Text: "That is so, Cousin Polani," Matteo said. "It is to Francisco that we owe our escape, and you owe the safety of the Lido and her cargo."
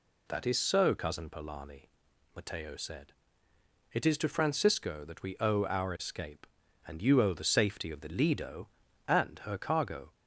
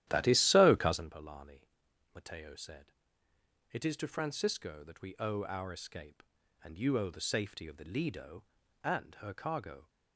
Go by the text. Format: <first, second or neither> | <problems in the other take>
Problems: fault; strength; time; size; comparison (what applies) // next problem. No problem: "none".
first | starts louder than the rest; strong; until 1.1 s; 12.5 dB